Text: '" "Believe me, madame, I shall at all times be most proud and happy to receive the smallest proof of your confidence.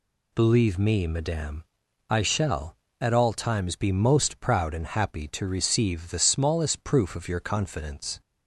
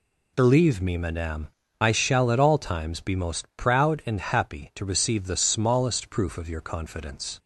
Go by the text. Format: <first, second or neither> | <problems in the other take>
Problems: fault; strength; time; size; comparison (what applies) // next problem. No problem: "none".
neither | none